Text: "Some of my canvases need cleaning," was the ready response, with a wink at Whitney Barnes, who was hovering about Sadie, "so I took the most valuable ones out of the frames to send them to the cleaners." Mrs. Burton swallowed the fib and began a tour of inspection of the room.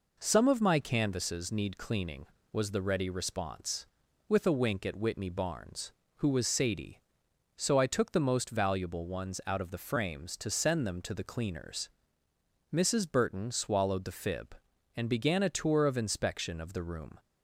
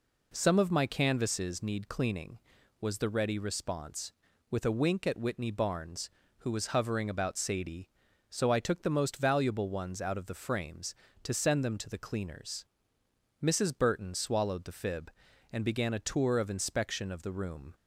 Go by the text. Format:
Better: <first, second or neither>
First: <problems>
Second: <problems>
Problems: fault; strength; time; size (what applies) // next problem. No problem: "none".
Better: second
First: skips "hovering about"; at 6.4 s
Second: none